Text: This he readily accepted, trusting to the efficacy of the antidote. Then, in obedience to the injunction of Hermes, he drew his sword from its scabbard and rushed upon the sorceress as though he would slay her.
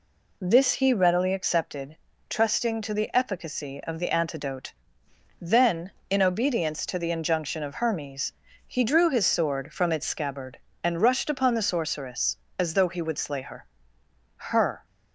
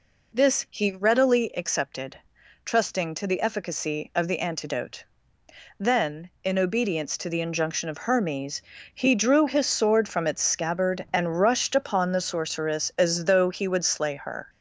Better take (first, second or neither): second